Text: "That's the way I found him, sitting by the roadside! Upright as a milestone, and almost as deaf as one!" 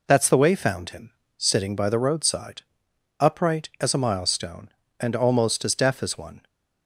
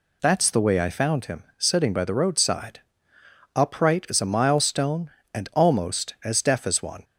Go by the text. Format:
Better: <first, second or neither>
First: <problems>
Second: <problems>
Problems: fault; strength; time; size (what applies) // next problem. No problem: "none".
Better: second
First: skips "I"; at 0.5 s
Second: none